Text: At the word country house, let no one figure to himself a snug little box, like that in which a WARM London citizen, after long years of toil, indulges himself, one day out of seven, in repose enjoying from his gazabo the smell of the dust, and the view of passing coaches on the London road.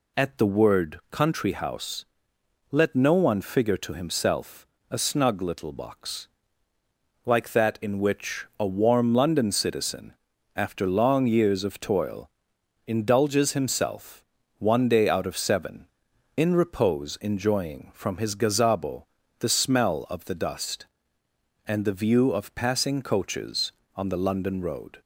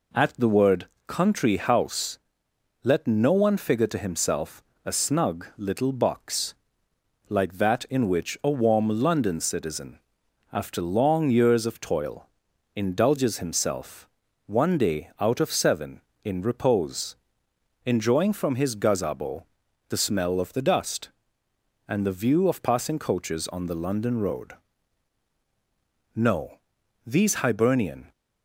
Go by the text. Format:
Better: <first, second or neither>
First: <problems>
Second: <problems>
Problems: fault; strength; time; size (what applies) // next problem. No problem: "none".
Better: first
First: pauses between "himself" and "a"; slight; at 4.6 s; 0.24 s long // pauses between "gazabo" and "the"; slight; at 19.0 s; 0.34 s long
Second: pauses between "word" and "country"; slight; at 0.8 s; 0.20 s long // pauses between "himself" and "a"; slight; at 4.6 s; 0.22 s long // pauses between "repose" and "enjoying"; noticeable; at 17.1 s; 0.68 s long // pauses between "gazabo" and "the"; noticeable; at 19.4 s; 0.46 s long // goes on to say "No these Hibernian"; strong; from 26.1 s on; 1.9 s long